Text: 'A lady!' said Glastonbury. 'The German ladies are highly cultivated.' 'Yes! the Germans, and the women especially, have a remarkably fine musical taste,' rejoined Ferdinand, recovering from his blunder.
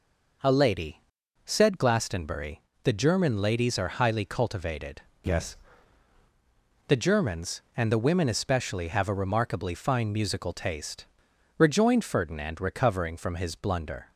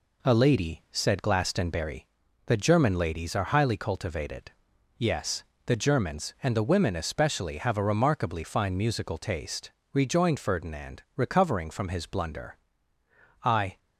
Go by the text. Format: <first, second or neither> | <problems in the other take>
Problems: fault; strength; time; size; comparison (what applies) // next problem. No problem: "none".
first | goes on to say "I"; slight; from 13.4 s on; 0.34 s long